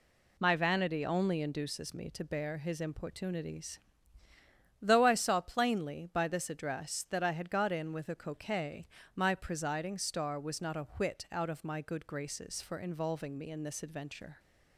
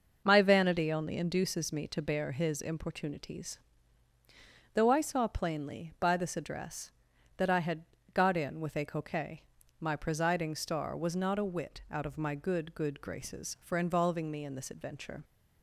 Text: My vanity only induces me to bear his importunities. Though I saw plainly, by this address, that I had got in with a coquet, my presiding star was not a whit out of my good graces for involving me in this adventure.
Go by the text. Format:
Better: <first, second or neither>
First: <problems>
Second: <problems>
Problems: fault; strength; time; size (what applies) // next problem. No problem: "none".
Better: first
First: none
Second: pauses between "had" and "got"; slight; at 7.8 s; 0.30 s long // says "good" twice; at 12.7 s